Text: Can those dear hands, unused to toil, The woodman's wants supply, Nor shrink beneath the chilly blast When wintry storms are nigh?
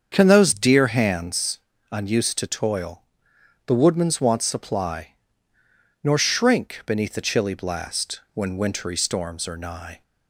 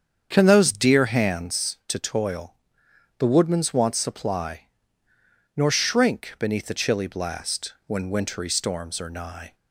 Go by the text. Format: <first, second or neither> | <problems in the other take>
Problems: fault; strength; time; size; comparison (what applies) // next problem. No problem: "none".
first | starts louder than the rest; strong; until 1.3 s; 7.5 dB; strong in the first // skips "unused"; at 1.8 s